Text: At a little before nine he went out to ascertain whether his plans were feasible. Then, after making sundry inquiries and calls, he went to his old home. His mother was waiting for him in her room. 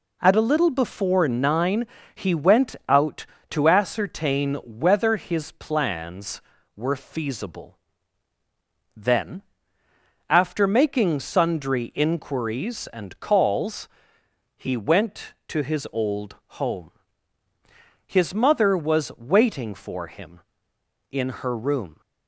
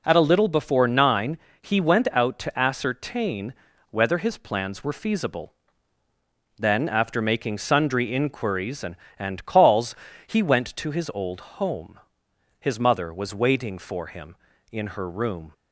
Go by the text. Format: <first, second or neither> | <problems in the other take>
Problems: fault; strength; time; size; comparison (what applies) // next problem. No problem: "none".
first | pauses between "nine" and "he"; slight; at 1.3 s; 0.24 s long; slight in the first // pauses between "ascertain" and "whether"; at 3.5 s; 0.38 s long // says "and" twice; at 9.1 s // pauses between "old" and "home"; slight; at 11.4 s; 0.20 s long; slight in the first